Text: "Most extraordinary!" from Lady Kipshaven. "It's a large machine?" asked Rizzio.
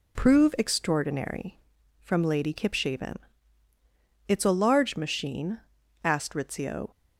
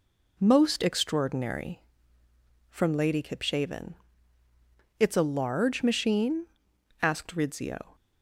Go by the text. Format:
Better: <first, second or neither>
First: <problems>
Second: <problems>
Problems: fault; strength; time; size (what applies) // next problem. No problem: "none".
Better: second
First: says "Prove" for "Most"; at 0.1 s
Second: none